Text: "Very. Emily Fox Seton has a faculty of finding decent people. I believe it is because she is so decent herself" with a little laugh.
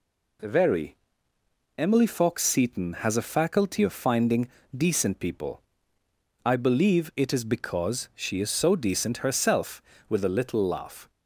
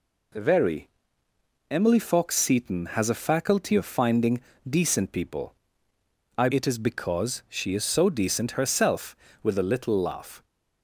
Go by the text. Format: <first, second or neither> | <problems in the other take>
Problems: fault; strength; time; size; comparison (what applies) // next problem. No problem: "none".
first | pauses between "finding" and "decent"; slight; at 4.4 s; 0.26 s long; slight in the first // skips "believe"; at 6.4 s